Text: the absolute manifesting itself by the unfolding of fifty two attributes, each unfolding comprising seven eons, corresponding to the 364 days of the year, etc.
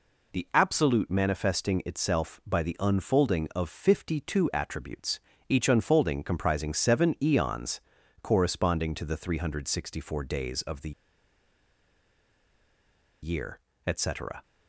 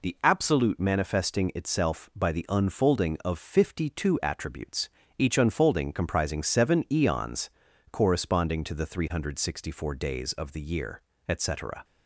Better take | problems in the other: second | pauses between "the" and "year"; strong; at 10.9 s; 2.3 s long

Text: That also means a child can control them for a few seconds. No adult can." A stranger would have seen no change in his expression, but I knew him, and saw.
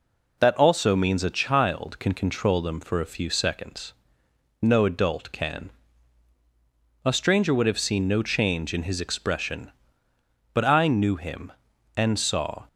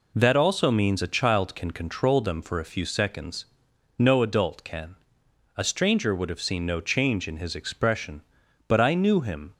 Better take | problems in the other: first | stops before "and saw"; at 9.5 s

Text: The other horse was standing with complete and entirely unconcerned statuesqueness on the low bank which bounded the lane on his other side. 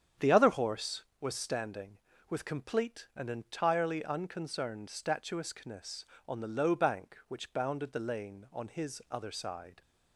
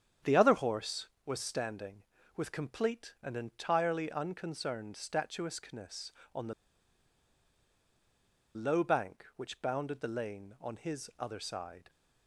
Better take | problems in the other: first | starts louder than the rest; strong; until 1.4 s; 8.5 dB; strong in the first // pauses between "the" and "low"; strong; at 6.5 s; 2.0 s long

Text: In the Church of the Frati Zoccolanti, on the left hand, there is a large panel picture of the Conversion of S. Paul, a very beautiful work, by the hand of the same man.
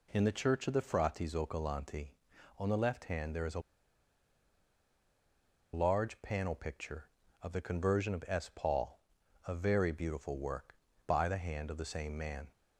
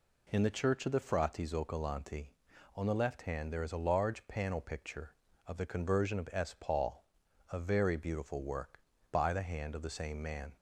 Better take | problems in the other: second | pauses between "a" and "large"; strong; at 3.5 s; 2.1 s long

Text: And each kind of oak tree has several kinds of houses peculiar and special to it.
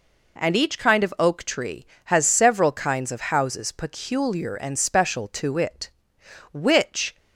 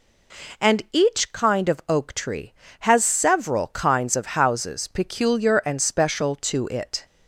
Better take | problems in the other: second | goes on to say "Which"; noticeable; from 6.5 s on; 0.64 s long

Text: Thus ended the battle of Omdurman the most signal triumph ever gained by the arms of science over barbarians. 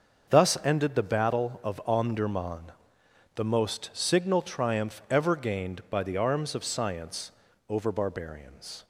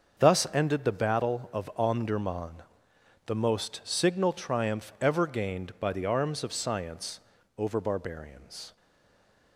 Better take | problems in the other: first | starts louder than the rest; until 1.2 s; 6.5 dB; also in the first // pauses between "Omdurman" and "the"; noticeable; at 2.6 s; 0.64 s long; noticeable in the first // pauses between "science" and "over"; at 7.1 s; 0.38 s long; also in the first // stays silent after the last word; slight; from 8.7 s on; 0.8 s long

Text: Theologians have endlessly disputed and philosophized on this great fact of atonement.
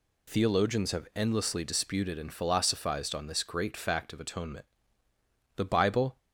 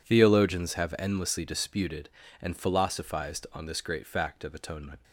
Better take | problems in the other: second | goes on to say "The Bible"; noticeable; from 5.5 s on; 0.62 s long

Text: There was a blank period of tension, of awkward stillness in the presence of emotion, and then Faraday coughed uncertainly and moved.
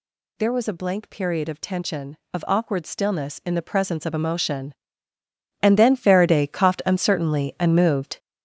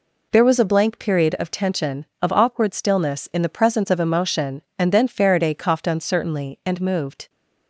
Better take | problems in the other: second | gets louder; strong; throughout; 7.5 dB

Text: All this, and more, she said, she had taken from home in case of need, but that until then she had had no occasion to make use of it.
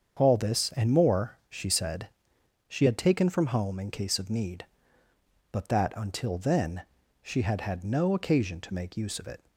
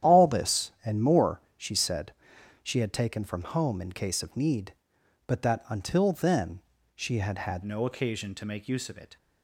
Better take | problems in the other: first | starts louder than the rest; strong; until 1.1 s; 10.5 dB; strong in the first // pauses between "then" and "she"; slight; at 6.5 s; 0.34 s long; also in the first // changes voice at "no"; from 7.6 s on; 1.5 s long

